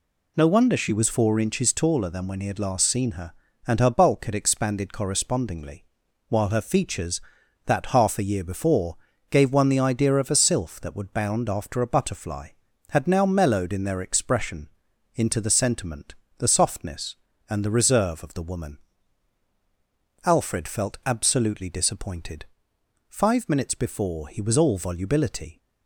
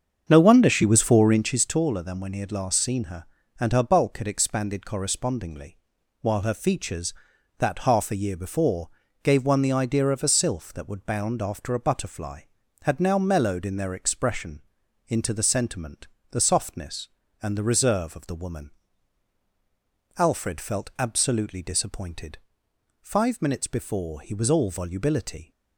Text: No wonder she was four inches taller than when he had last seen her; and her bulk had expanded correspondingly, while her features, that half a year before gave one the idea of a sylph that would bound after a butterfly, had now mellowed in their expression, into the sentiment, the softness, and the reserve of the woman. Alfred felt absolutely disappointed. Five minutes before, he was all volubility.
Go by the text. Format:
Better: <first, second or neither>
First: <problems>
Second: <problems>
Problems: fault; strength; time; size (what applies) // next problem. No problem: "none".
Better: first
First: pauses between "before" and "gave"; slight; at 8.9 s; 0.34 s long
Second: starts louder than the rest; strong; until 1.6 s; 7 dB // pauses between "before" and "gave"; slight; at 8.8 s; 0.34 s long